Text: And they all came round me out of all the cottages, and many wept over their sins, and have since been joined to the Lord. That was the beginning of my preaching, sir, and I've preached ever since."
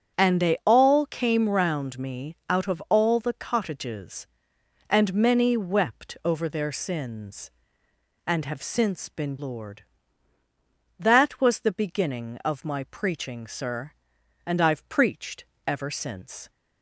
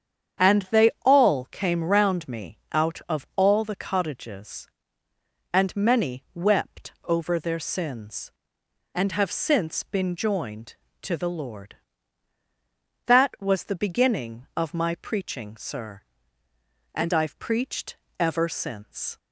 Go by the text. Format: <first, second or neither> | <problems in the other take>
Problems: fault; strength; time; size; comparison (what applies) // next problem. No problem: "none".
second | starts louder than the rest; strong; until 1.2 s; 8.5 dB; strong in the second // skips "joined to the"; at 9.3 s // pauses between "preached" and "ever"; slight; at 15.4 s; 0.20 s long; slight in the second